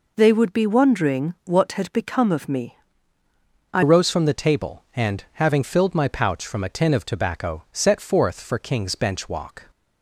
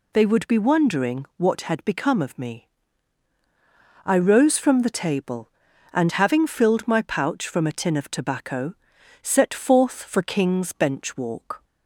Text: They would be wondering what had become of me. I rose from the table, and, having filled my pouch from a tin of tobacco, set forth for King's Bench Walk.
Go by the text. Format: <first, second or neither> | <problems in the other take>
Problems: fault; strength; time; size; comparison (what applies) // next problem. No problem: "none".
second | changes voice at "rose"; from 3.8 s on; 5.9 s long